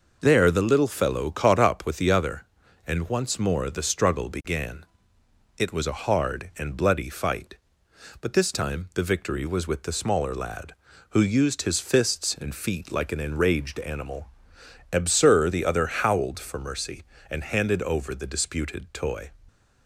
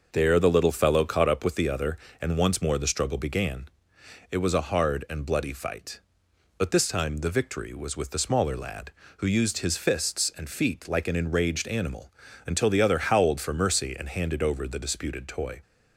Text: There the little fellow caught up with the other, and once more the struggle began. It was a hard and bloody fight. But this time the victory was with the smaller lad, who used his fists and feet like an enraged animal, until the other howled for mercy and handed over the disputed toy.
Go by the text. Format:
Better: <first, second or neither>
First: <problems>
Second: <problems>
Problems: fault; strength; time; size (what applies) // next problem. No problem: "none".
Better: second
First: says "absur" for "until"; at 14.9 s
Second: none